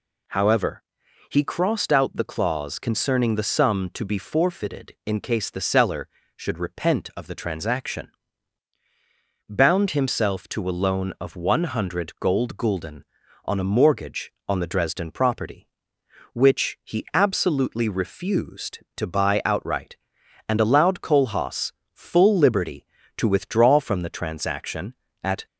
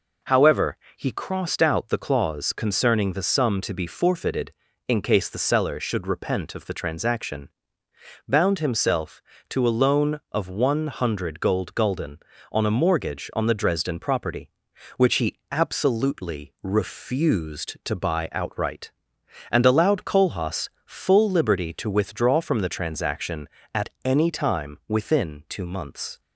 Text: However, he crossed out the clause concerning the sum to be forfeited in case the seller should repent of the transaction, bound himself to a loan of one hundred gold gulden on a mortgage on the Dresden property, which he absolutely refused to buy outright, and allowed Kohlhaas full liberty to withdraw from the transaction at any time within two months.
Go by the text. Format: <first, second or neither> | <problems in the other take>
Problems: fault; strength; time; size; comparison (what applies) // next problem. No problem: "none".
second | pauses between "Kohlhaas" and "full"; slight; at 21.7 s; 0.22 s long; slight in the second // stops before "any time within two months"; at 25.4 s